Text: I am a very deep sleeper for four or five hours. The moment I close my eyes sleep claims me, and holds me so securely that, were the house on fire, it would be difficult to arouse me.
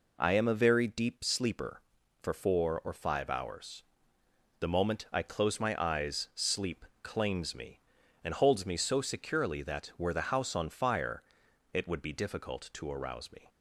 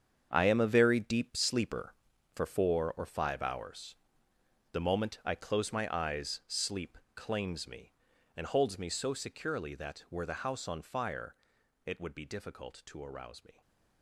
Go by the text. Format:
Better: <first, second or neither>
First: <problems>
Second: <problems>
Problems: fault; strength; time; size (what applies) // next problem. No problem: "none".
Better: first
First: pauses between "sleep" and "claims"; slight; at 6.8 s; 0.16 s long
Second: gets quieter; strong; throughout; 11.5 dB // pauses between "sleep" and "claims"; slight; at 6.9 s; 0.16 s long // stays silent after the last word; slight; from 13.5 s on; 0.5 s long